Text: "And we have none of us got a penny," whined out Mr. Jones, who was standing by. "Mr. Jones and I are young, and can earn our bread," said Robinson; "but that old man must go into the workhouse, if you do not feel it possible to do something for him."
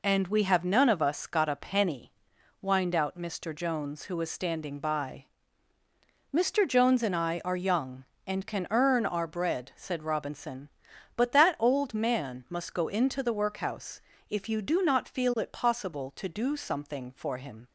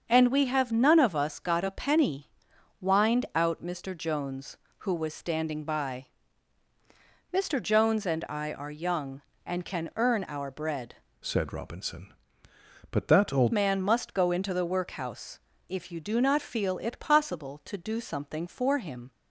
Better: first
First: none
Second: starts louder than the rest; until 1.0 s; 6.5 dB // changes voice from "said" to "old"; from 11.2 to 13.5 s; 2.3 s long

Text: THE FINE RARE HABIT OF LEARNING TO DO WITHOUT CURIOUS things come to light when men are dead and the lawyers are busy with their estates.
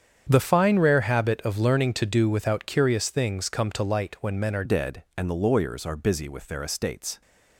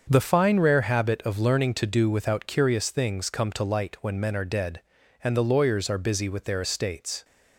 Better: second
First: starts louder than the rest; strong; until 1.3 s; 8 dB // changes voice at "dead"; from 4.6 s on; 2.6 s long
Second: starts louder than the rest; until 1.1 s; 6.5 dB

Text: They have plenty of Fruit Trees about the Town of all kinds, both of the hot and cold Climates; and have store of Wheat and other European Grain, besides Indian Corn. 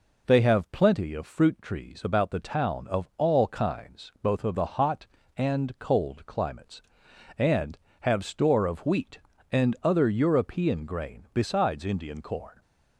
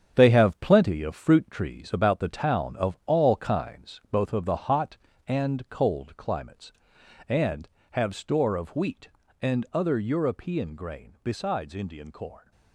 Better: first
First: none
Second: gets quieter; strong; throughout; 8 dB

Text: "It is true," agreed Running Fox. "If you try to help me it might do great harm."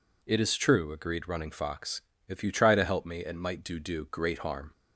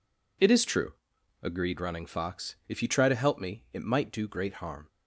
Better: second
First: says "do" twice; at 3.7 s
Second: none

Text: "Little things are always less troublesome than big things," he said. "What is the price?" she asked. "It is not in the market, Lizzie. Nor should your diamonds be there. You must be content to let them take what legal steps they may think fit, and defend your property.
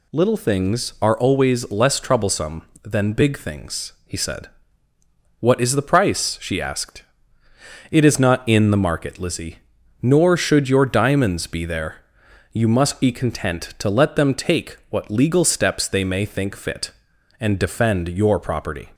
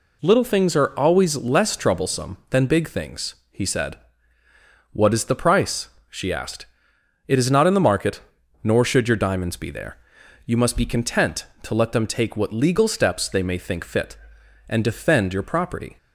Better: first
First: none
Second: skips "Lizzie"; at 8.4 s

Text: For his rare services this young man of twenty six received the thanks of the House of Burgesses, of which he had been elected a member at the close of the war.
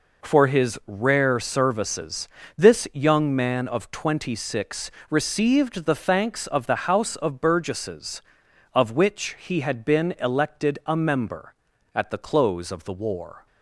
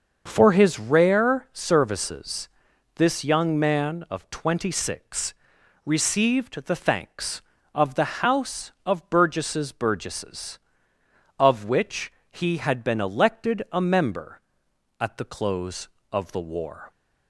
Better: first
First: pauses between "services" and "this"; slight; at 2.2 s; 0.28 s long // pauses between "six" and "received"; slight; at 4.9 s; 0.18 s long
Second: starts louder than the rest; until 1.2 s; 6.5 dB // pauses between "services" and "this"; noticeable; at 2.4 s; 0.48 s long // pauses between "six" and "received"; noticeable; at 5.3 s; 0.52 s long // says "Burgesses" twice; at 9.7 s // pauses between "which" and "he"; slight; at 12.1 s; 0.18 s long

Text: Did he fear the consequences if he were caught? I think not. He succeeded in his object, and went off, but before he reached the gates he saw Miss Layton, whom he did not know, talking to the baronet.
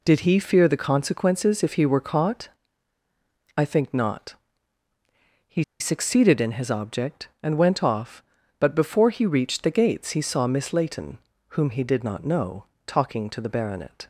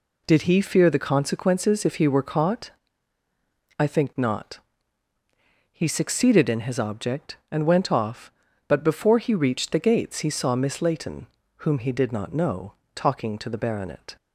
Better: second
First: pauses between "He" and "succeeded"; slight; at 5.6 s; 0.16 s long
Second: none

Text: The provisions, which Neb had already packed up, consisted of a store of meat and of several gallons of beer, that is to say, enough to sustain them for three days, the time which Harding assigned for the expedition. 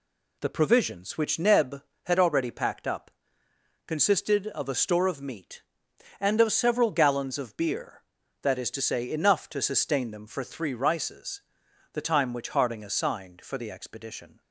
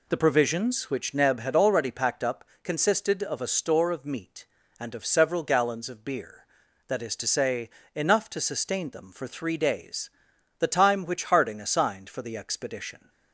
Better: second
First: says "rices" for "days"; at 10.7 s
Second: none

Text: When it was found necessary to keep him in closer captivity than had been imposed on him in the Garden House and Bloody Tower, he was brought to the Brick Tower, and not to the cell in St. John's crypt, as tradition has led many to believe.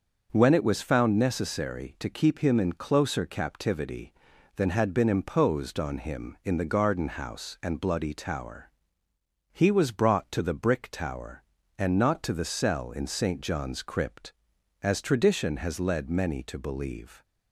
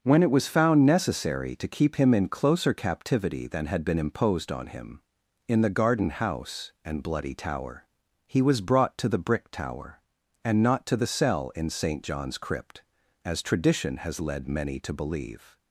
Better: neither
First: starts louder than the rest; noticeable; until 1.3 s; 6 dB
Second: starts louder than the rest; until 1.0 s; 6.5 dB

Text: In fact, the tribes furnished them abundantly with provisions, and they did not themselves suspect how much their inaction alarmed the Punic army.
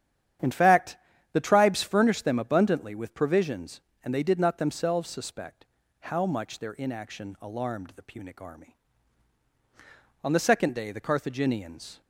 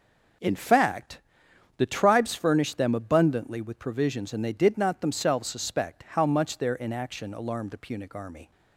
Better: second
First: starts louder than the rest; strong; until 1.7 s; 10 dB // pauses between "suspect" and "how"; slight; at 5.6 s; 0.36 s long // goes on to say "On the second day the Carthaginians"; strong; from 10.2 s on; 1.7 s long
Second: none

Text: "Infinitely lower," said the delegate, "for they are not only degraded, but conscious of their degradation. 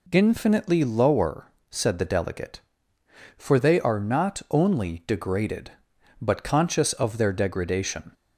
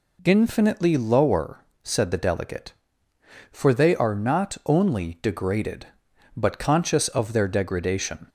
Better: neither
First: none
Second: none

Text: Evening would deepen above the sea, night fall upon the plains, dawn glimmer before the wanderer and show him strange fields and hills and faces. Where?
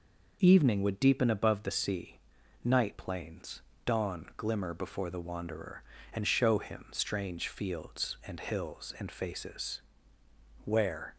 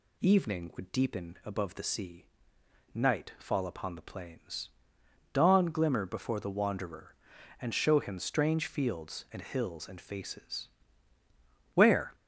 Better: second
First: skips "fall upon the"; at 2.9 s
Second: none

